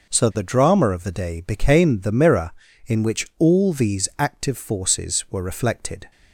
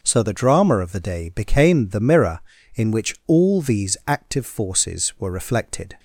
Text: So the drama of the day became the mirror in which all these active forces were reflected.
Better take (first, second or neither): neither